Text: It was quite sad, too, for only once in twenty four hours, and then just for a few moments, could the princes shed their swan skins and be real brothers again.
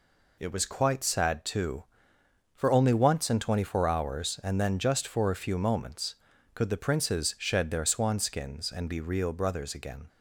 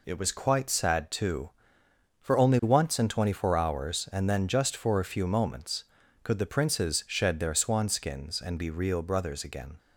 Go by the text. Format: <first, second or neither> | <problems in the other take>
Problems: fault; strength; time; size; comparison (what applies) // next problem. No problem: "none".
neither | none